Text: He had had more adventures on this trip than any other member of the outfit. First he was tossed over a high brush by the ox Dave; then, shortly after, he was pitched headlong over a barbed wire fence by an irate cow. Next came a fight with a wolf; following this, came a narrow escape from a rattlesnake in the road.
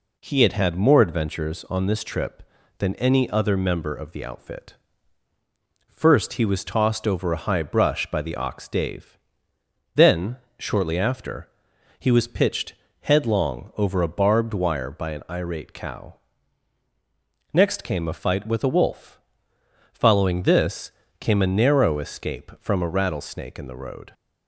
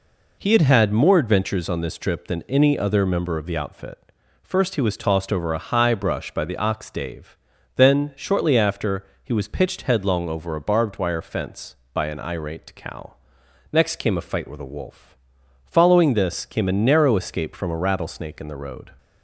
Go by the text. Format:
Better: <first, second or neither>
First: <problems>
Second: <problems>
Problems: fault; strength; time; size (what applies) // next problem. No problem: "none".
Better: second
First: pauses between "pitched" and "headlong"; slight; at 12.7 s; 0.28 s long // skips "fence"; at 14.9 s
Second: none